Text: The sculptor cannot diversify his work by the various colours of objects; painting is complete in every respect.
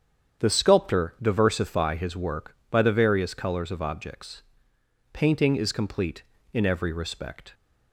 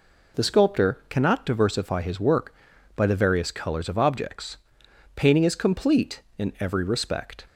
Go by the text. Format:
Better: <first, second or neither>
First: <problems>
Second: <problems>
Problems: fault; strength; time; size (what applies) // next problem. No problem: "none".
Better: second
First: starts louder than the rest; strong; until 1.4 s; 8.5 dB // skips "cannot"; at 1.1 s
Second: none